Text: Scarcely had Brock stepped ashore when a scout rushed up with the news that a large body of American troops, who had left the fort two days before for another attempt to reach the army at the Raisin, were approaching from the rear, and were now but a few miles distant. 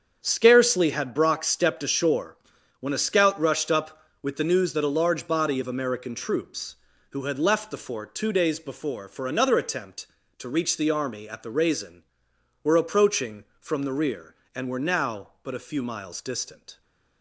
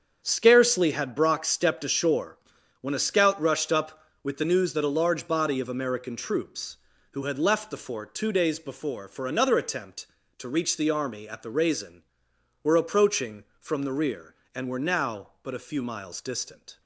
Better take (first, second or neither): neither